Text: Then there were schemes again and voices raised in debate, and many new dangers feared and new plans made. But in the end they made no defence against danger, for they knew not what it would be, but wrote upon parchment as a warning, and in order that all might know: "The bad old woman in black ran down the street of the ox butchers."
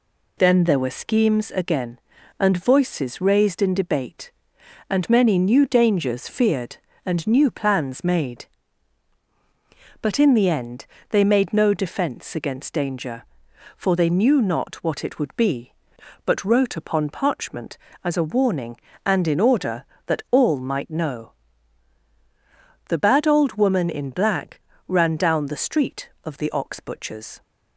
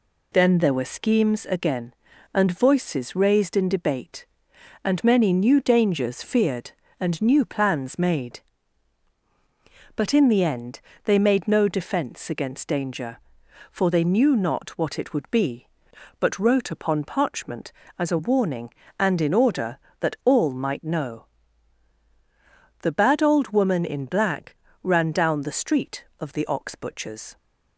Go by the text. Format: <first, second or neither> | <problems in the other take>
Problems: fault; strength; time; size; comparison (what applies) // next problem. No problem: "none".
neither | pauses between "end" and "they"; slight; the same in both // pauses between "black" and "ran"; slight; the same in both